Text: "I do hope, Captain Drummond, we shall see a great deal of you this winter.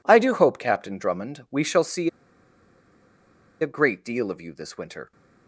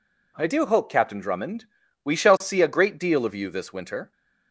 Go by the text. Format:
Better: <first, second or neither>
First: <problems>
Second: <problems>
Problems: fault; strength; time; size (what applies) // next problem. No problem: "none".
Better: second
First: pauses between "see" and "a"; strong; at 2.0 s; 1.5 s long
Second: none